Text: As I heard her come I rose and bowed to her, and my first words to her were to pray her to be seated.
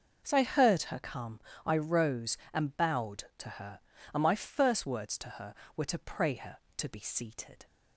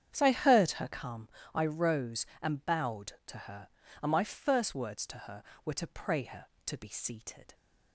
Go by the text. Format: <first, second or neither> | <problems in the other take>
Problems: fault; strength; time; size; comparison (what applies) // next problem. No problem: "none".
first | starts louder than the rest; strong; until 1.1 s; 8.5 dB // pauses between "come" and "I"; slight; at 1.2 s; 0.26 s long; slight in the first